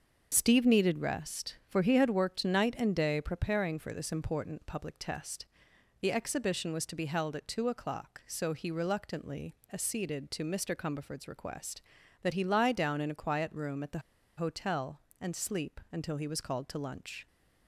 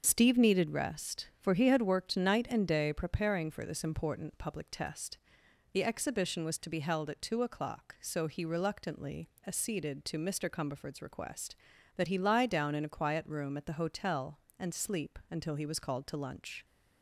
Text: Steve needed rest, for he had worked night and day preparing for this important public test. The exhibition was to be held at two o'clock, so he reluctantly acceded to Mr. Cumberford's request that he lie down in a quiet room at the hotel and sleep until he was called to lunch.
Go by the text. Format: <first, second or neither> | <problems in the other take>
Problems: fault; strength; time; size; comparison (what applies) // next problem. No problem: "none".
second | starts louder than the rest; noticeable; until 1.3 s; 6 dB; noticeable in the second // pauses between "reluctantly" and "acceded"; slight; at 9.5 s; 0.18 s long; slight in the second // pauses between "the" and "hotel"; at 13.9 s; 0.38 s long